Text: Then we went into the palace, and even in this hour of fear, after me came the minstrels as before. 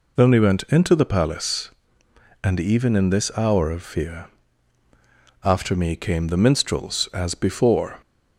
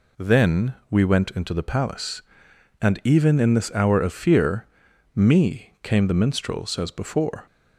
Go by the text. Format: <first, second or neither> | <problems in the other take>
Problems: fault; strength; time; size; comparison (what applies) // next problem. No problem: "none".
first | pauses between "Then" and "we"; slight; at 0.7 s; 0.16 s long // skips "after"; at 4.9 s